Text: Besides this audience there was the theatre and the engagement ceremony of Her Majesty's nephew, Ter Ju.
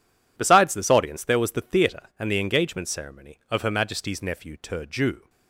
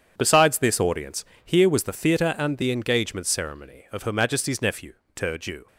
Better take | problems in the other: first | says "here" for "there"; at 1.4 s

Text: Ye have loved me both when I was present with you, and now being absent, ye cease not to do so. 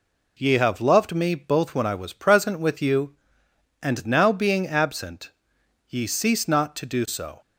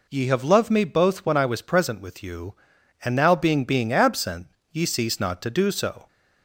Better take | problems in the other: first | says "being" twice; at 3.6 s

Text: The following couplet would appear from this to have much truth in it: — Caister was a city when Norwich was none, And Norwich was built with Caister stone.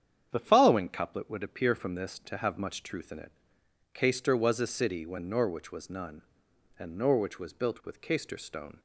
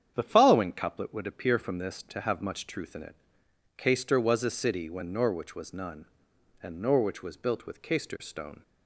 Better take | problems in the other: neither | starts louder than the rest; strong; the same in both

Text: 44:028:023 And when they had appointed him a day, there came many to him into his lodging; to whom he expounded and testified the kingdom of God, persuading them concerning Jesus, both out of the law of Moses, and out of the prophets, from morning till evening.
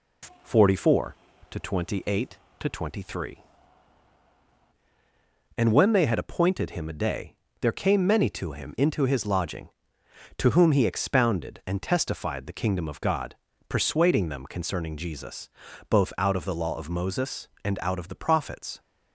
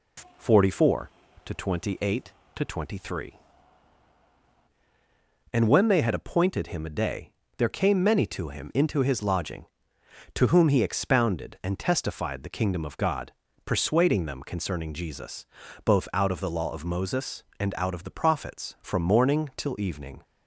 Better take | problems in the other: second | stops before "from morning till evening"; at 18.7 s

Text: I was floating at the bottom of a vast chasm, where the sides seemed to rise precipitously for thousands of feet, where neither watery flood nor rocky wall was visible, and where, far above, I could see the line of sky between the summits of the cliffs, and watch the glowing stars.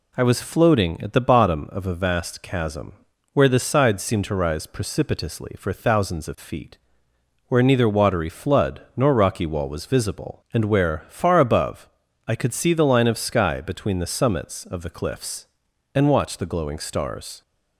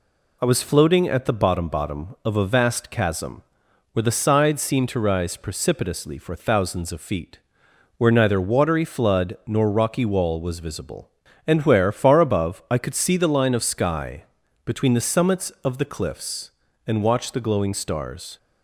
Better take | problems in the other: first | says "bottom" twice; at 1.6 s // pauses between "sky" and "between"; at 14.2 s; 0.38 s long

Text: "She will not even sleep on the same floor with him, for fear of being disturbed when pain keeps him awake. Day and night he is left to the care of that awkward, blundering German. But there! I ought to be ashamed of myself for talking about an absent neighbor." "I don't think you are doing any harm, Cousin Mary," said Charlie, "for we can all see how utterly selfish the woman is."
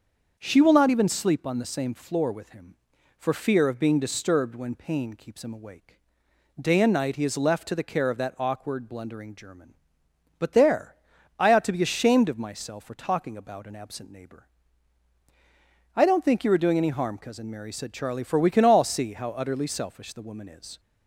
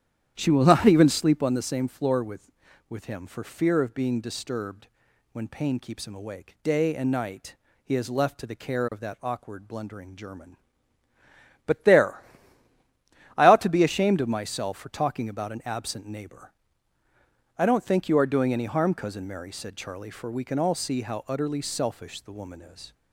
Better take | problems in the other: first | starts louder than the rest; strong; until 1.3 s; 10 dB; also in the first // says "with" twice; at 2.8 s // pauses between "disturbed" and "when"; noticeable; at 4.8 s; 0.46 s long // pauses between "night" and "he"; slight; at 7.5 s; 0.26 s long

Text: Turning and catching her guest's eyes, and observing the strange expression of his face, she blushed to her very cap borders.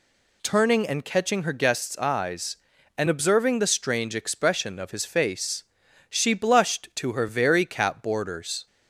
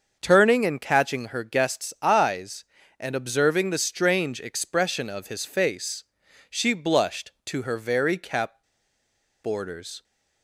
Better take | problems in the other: first | starts louder than the rest; until 1.2 s; 6.5 dB // pauses between "cap" and "borders"; noticeable; at 8.6 s; 0.79 s long

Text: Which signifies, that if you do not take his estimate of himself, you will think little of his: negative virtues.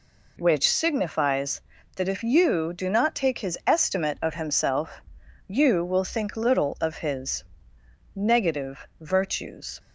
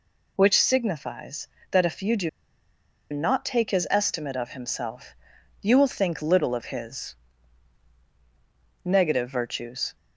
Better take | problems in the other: first | pauses between "do" and "not"; noticeable; at 2.2 s; 0.82 s long

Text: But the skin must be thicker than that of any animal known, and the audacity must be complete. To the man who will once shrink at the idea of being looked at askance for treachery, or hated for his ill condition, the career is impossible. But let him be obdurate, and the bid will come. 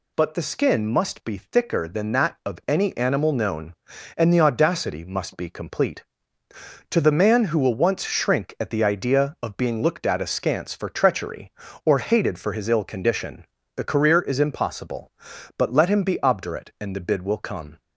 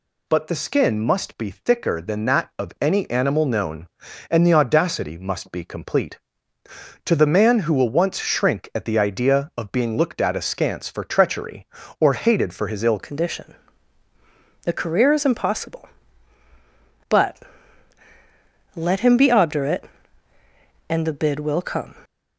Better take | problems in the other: first | changes voice at "condition"; from 12.9 s on; 9.0 s long // pauses between "But" and "let"; strong; at 17.3 s; 1.3 s long

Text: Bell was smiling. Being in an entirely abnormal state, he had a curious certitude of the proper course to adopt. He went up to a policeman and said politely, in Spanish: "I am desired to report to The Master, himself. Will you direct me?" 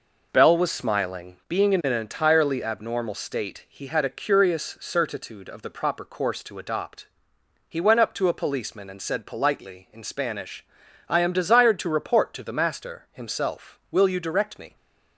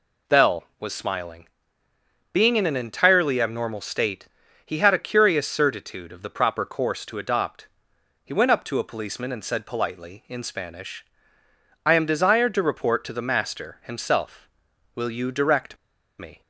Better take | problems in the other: first | pauses between "direct" and "me"; at 15.7 s; 0.43 s long

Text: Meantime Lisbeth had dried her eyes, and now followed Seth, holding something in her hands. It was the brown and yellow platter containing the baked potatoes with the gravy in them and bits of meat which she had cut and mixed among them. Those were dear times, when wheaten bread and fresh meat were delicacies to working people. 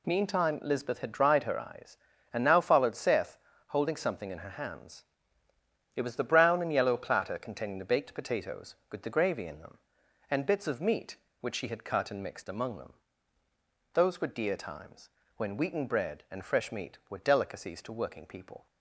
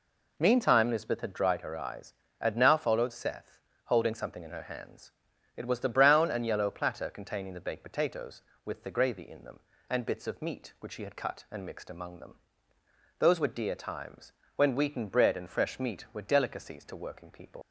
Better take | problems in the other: first | leaves "people" unfinished; at 17.6 s; 120 ms

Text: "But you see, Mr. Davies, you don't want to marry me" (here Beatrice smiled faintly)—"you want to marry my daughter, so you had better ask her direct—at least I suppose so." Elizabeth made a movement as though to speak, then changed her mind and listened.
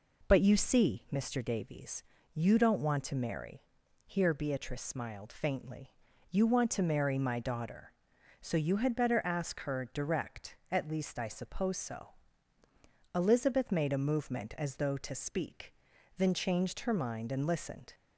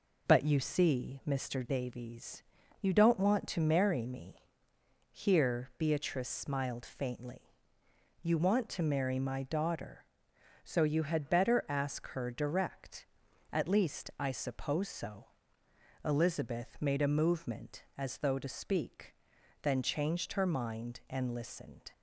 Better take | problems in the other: second | skips "me"; at 3.8 s

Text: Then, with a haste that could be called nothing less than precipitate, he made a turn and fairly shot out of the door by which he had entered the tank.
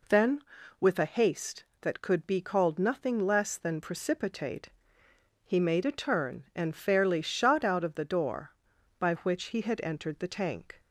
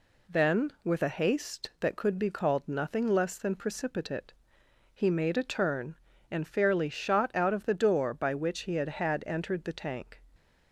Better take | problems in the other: first | says "had" twice; at 8.9 s

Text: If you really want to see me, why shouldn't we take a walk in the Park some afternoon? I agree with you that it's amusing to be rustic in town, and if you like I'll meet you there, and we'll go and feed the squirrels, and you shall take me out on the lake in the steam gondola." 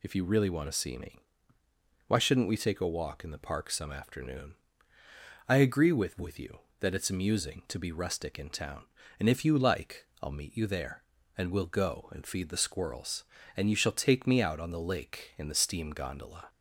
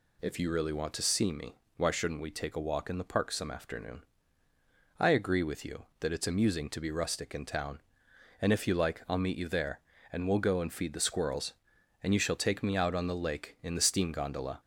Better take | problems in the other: second | says "with" twice; at 6.1 s // pauses between "like" and "I'll"; slight; at 10.0 s; 0.16 s long

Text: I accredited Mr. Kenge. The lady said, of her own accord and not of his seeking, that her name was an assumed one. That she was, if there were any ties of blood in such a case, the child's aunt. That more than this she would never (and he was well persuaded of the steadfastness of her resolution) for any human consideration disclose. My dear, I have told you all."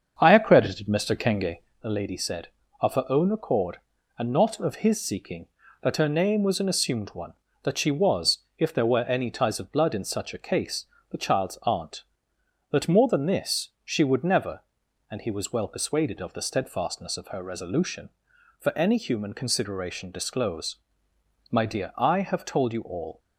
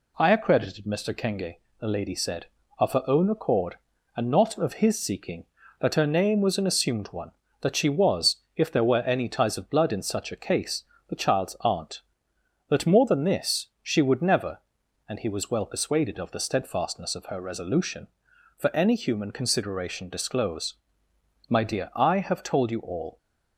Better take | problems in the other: second | starts louder than the rest; until 1.8 s; 7 dB

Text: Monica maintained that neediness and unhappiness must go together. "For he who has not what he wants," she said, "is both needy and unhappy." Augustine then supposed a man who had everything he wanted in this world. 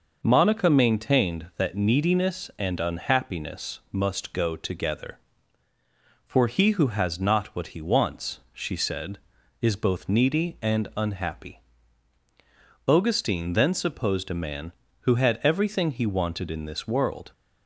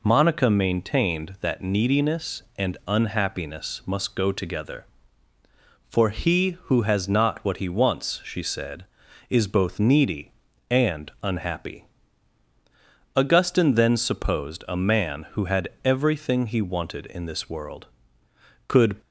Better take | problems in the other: first | pauses between "had" and "everything"; slight; at 15.6 s; 0.16 s long // goes on to say "Could"; slight; from 18.6 s on; 0.32 s long

